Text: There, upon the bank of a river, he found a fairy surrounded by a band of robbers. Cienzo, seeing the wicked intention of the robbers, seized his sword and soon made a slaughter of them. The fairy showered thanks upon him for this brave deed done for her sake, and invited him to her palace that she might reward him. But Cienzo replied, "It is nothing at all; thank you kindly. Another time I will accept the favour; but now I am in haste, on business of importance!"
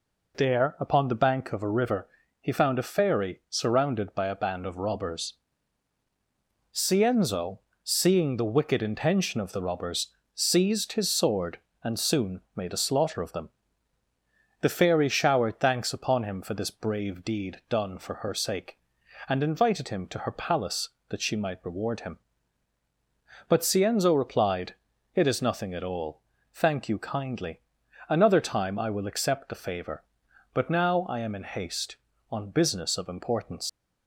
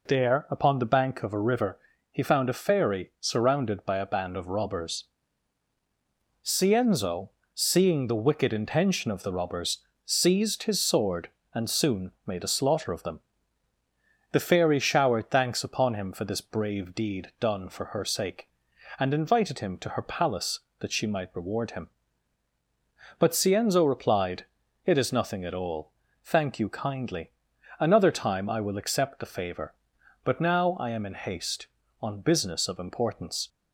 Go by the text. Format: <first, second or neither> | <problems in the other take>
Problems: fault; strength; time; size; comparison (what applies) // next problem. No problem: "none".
second | leaves "importance" unfinished; at 33.6 s; 80 ms